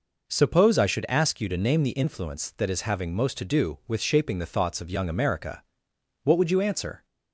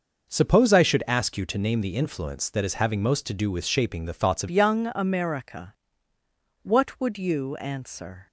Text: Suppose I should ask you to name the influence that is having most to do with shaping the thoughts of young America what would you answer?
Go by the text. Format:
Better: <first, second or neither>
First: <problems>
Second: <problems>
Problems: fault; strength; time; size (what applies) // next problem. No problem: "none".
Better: first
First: pauses between "America" and "what"; noticeable; at 5.6 s; 0.60 s long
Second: changes voice at "young"; from 4.5 s on; 3.7 s long // pauses between "America" and "what"; noticeable; at 5.7 s; 0.88 s long